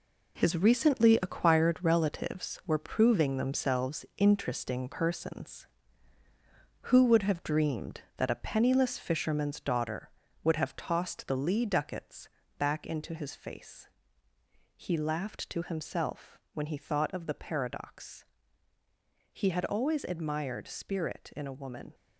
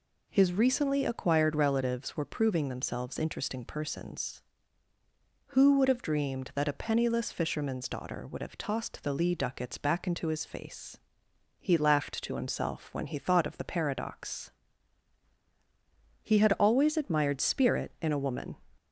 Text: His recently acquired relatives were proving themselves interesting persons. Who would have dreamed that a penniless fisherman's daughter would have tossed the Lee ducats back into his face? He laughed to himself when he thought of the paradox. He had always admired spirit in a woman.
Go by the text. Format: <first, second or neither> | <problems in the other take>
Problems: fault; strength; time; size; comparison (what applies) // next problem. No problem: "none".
second | gets quieter; strong; throughout; 8.5 dB // pauses between "ducats" and "back"; slight; at 12.2 s; 0.30 s long